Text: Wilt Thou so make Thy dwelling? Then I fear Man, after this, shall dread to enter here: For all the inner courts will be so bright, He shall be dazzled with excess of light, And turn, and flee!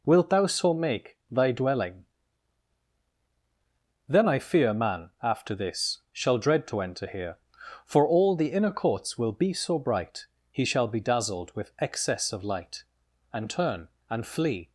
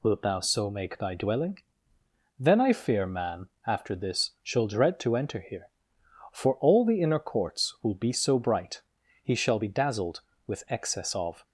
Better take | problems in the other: first | stops before "light And turn and flee"; at 11.4 s

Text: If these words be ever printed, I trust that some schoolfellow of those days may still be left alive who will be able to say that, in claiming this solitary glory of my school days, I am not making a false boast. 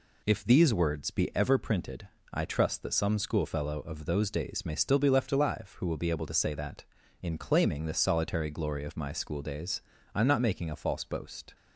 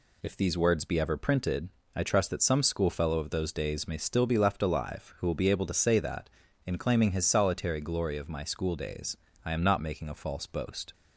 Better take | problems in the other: first | says "his" for "this"; at 7.1 s

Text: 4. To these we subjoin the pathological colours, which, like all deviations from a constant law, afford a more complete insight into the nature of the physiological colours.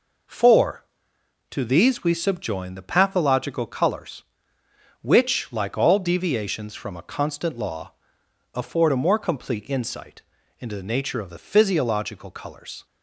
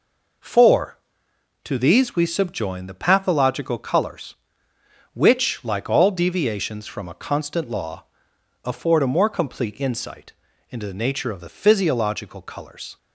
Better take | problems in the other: neither | pauses between "insight" and "into"; slight; the same in both

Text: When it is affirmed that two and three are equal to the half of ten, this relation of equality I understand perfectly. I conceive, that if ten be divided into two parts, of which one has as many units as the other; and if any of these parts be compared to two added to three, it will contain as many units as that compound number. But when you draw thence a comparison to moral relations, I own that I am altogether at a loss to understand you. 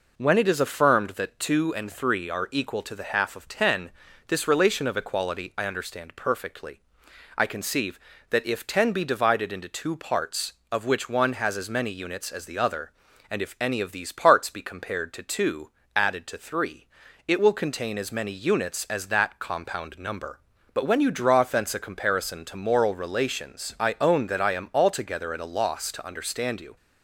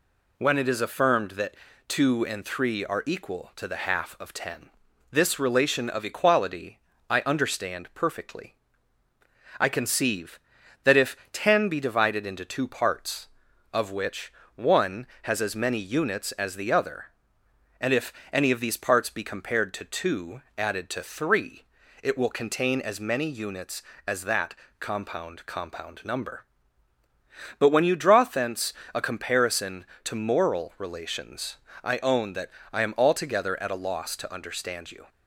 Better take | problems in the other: first | pauses between "that" and "two"; slight; at 1.5 s; 0.32 s long // pauses between "equality" and "I"; slight; at 6.7 s; 0.30 s long // pauses between "if" and "ten"; slight; at 11.1 s; 0.16 s long // pauses between "which" and "one"; slight; at 14.3 s; 0.24 s long // pauses between "if" and "any"; slight; at 18.1 s; 0.20 s long // pauses between "two" and "added"; slight; at 20.4 s; 0.16 s long; slight in the first // pauses between "that" and "compound"; slight; at 24.5 s; 0.24 s long // says "compound" twice; at 25.4 s // pauses between "thence" and "a"; slight; at 28.7 s; 0.20 s long // pauses between "that" and "I"; slight; at 32.5 s; 0.22 s long

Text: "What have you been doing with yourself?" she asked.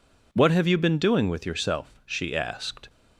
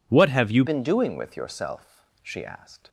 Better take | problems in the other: first | changes voice at "been"; from 0.6 s on; 2.2 s long

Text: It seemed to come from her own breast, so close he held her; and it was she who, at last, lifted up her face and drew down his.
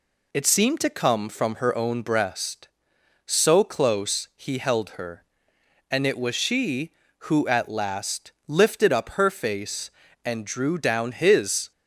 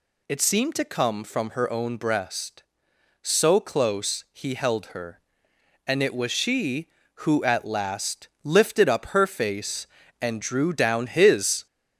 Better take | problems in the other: first | gets louder; throughout; 3.5 dB

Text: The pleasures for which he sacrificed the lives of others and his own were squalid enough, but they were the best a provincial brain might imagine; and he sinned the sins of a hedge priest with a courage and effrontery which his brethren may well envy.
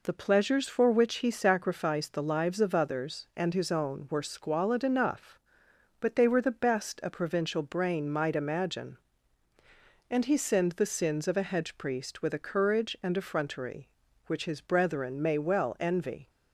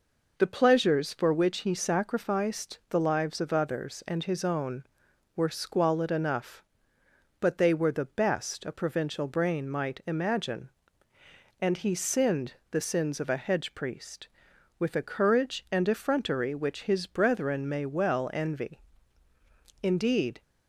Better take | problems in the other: first | pauses between "sinned" and "the"; slight; at 12.5 s; 0.16 s long // goes on to say "Indeed"; from 19.8 s on; 0.60 s long

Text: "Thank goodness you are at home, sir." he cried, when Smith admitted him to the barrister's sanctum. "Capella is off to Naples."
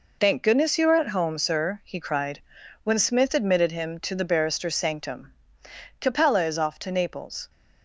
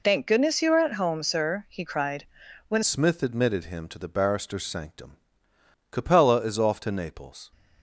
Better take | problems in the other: first | changes voice at "Smith"; from 2.8 s on; 4.7 s long

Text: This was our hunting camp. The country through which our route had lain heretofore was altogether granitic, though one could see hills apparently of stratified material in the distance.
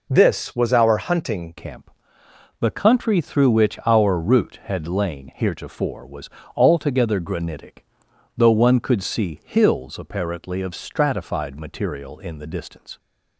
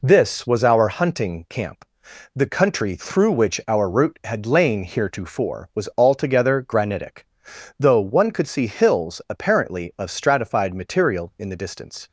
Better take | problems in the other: second | changes voice at "camp"; from 1.5 s on; 11.4 s long // pauses between "was" and "altogether"; slight; at 6.2 s; 0.28 s long

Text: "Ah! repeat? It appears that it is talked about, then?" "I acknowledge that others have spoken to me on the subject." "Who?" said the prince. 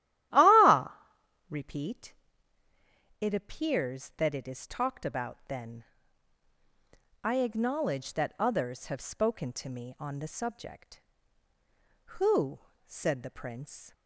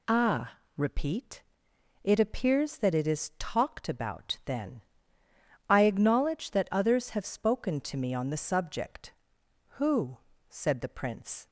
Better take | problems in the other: second | starts louder than the rest; strong; until 1.6 s; 13.5 dB

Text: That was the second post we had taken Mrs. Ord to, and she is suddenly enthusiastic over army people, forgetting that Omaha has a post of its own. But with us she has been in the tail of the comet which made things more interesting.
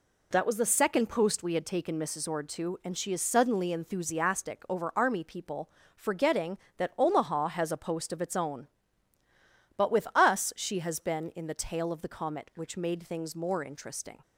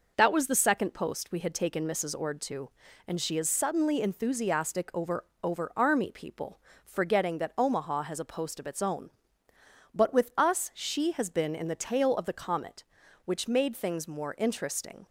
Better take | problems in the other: first | says "over" twice; at 5.4 s

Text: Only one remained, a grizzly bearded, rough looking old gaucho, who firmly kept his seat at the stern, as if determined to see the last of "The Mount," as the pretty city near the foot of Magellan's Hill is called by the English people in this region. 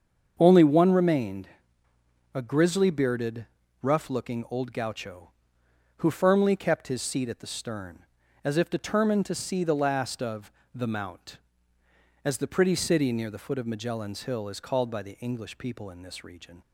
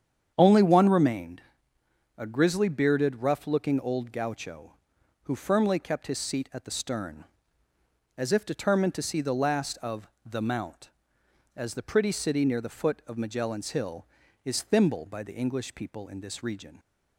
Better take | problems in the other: first | starts louder than the rest; strong; until 1.3 s; 8.5 dB; also in the first // pauses between "of" and "The"; slight; at 10.0 s; 0.16 s long; slight in the first // says "thimble" for "called"; at 14.6 s

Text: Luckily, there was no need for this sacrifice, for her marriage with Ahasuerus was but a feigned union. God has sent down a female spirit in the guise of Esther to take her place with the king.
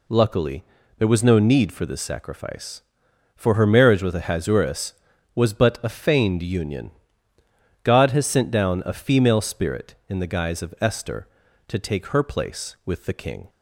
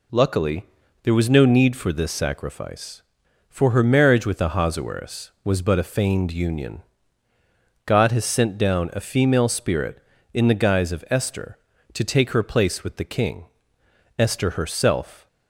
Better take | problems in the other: first | goes on to say "Esther herself"; noticeable; from 14.1 s on; 1.0 s long

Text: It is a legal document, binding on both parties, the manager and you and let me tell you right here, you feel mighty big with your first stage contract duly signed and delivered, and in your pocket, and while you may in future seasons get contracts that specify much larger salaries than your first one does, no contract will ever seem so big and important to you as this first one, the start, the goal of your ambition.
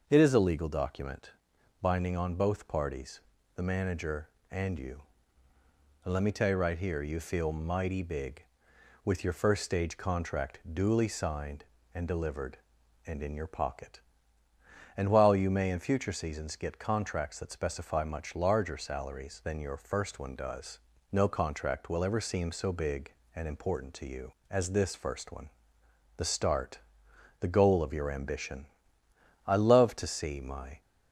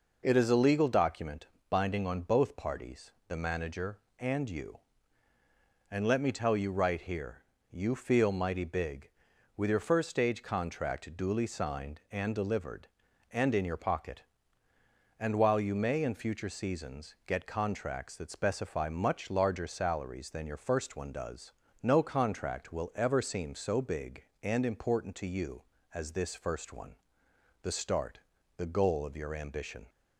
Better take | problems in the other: second | starts louder than the rest; noticeable; until 1.0 s; 6 dB // goes on to say "I love to see my"; from 29.4 s on; 1.3 s long

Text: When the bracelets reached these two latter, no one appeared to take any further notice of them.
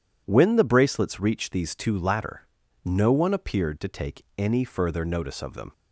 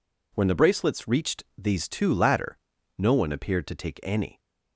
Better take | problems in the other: first | pauses between "reached" and "these"; slight; at 1.4 s; 0.16 s long // stops before "further notice of them"; at 4.3 s

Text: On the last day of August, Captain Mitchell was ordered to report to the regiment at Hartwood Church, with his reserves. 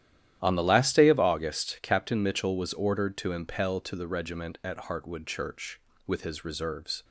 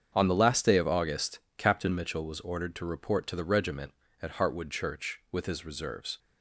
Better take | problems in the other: second | starts louder than the rest; strong; until 1.4 s; 12 dB; strong in the second // says "impel" for "report"; at 3.3 s

